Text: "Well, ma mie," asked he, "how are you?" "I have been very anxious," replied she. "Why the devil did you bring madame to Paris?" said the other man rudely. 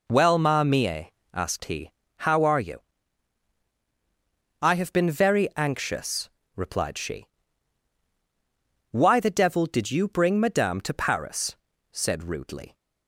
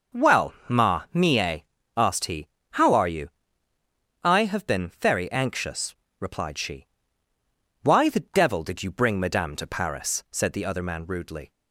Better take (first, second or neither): second